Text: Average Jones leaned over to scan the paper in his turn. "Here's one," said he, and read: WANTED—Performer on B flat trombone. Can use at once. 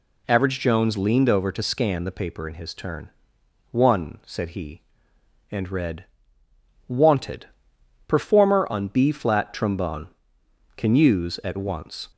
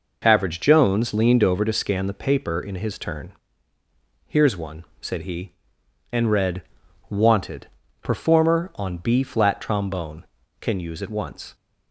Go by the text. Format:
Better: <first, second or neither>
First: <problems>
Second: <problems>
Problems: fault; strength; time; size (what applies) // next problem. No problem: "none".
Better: second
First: skips "Here's"; at 3.4 s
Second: none